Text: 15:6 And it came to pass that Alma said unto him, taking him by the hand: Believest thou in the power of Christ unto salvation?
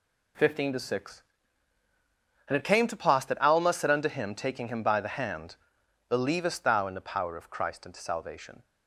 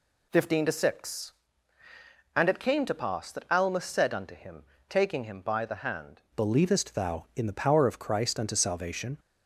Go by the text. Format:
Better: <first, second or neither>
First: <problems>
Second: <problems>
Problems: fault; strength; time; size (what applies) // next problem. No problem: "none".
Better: first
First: none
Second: changes voice at "Believest"; from 6.3 s on; 2.8 s long